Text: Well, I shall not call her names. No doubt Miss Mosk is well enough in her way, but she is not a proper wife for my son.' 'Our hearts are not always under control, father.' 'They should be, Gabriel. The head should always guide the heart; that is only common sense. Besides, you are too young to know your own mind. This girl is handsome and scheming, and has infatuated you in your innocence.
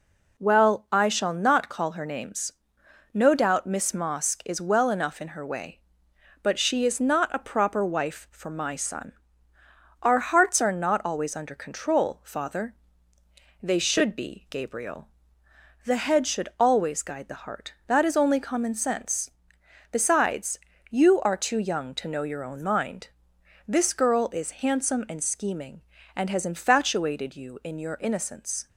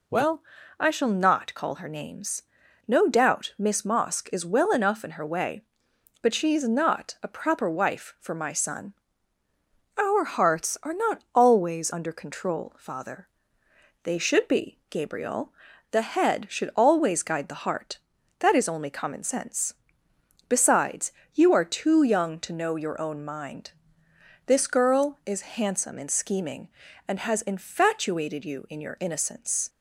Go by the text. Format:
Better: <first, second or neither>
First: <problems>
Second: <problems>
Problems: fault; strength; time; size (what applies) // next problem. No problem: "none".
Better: neither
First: none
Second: none